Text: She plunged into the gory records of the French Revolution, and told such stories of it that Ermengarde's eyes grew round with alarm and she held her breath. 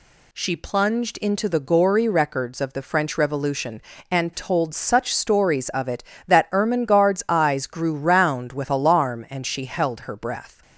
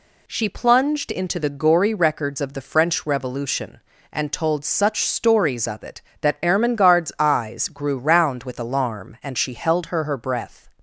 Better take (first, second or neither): first